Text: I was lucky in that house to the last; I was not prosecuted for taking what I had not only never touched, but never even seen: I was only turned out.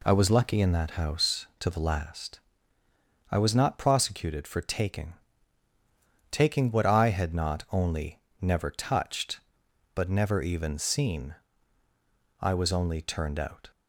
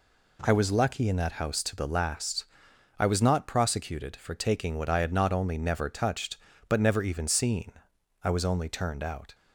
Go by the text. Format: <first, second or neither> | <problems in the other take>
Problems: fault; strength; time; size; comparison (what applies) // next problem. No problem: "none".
second | says "taking" twice; at 6.3 s // pauses between "only" and "never"; slight; at 8.1 s; 0.22 s long